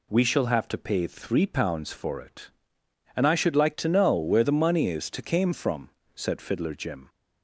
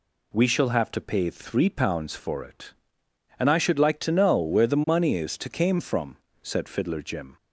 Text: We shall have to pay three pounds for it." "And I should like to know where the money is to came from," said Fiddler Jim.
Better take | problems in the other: neither | none

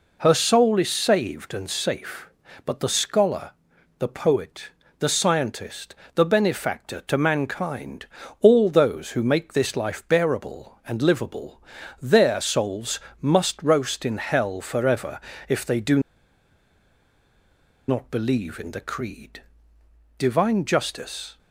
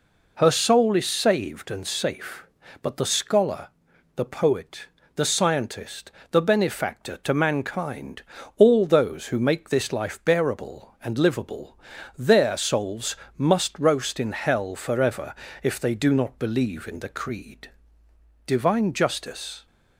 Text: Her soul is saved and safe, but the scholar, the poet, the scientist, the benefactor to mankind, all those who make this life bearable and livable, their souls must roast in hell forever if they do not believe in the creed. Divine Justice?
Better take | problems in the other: second | pauses between "souls" and "must"; slight; at 12.9 s; 0.24 s long; slight in the second // pauses between "forever" and "if"; slight; at 15.1 s; 0.28 s long; slight in the second // pauses between "do" and "not"; strong; at 15.9 s; 1.8 s long

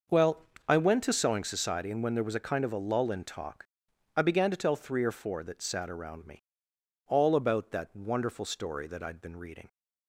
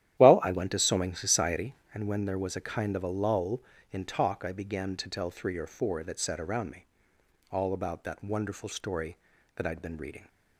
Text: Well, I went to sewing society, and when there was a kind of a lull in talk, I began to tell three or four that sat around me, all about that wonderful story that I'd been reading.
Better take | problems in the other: first | starts louder than the rest; strong; until 2.1 s; 12 dB

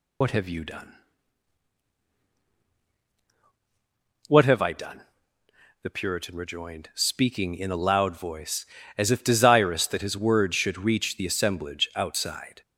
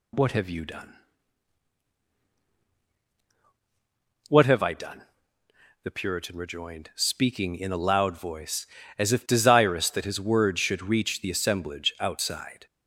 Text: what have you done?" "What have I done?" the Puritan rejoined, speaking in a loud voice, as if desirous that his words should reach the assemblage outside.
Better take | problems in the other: second | loses the start of "what"; at 0.2 s; 80 ms

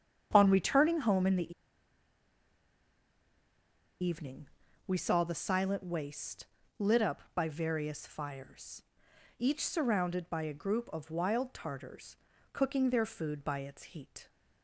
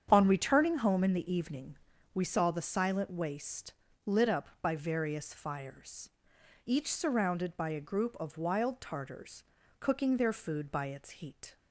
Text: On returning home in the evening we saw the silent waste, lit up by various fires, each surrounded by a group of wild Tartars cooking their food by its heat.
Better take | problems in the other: second | starts louder than the rest; strong; until 1.3 s; 8 dB; strong in the second // pauses between "the" and "evening"; strong; at 1.5 s; 2.5 s long // pauses between "evening" and "we"; at 4.4 s; 0.40 s long; also in the second // pauses between "Tartars" and "cooking"; at 12.1 s; 0.38 s long; also in the second

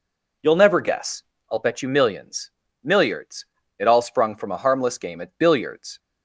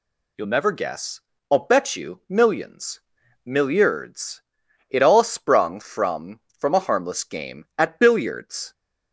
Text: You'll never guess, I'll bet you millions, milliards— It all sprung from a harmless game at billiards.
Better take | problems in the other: first | says "from" twice; at 6.5 s

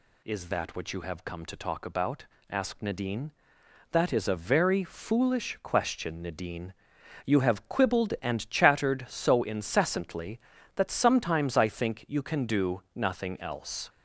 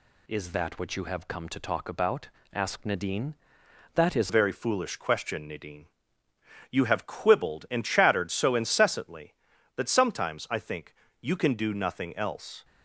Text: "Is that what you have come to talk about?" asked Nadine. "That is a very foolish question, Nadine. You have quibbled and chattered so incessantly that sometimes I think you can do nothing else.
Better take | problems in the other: first | changes voice at "a"; from 4.2 s on; 8.4 s long // pauses between "think" and "you"; slight; at 10.9 s; 0.30 s long

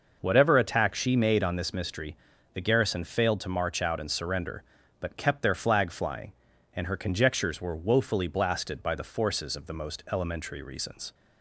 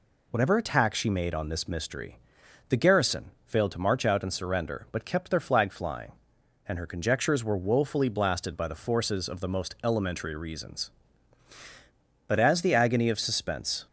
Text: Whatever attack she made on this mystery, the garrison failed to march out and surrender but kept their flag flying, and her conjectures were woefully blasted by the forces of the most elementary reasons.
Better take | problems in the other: first | pauses between "garrison" and "failed"; slight; at 3.3 s; 0.16 s long // goes on to say "But as the agony of suspense"; from 12.2 s on; 1.6 s long

